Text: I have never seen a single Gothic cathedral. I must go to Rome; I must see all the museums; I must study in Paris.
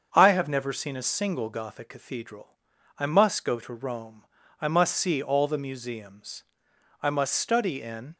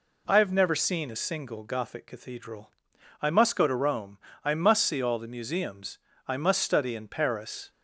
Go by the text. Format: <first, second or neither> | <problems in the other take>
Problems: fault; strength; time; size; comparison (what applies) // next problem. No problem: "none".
second | starts louder than the rest; until 1.1 s; 7 dB // stops before "Paris"; at 8.1 s